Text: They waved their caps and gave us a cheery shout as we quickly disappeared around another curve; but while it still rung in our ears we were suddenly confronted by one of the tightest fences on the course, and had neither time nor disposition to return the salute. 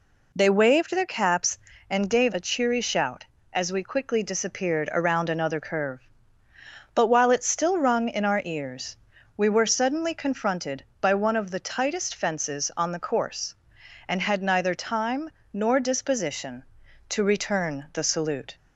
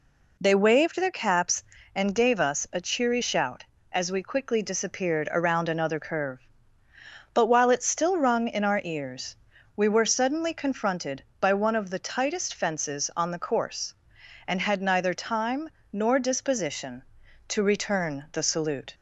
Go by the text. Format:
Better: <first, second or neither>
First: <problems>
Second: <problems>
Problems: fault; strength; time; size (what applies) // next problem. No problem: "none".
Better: second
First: skips "us"; at 2.3 s // pauses between "ears" and "we"; at 8.9 s; 0.42 s long // pauses between "time" and "nor"; slight; at 15.3 s; 0.20 s long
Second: pauses between "ears" and "we"; at 9.3 s; 0.42 s long // pauses between "time" and "nor"; slight; at 15.7 s; 0.20 s long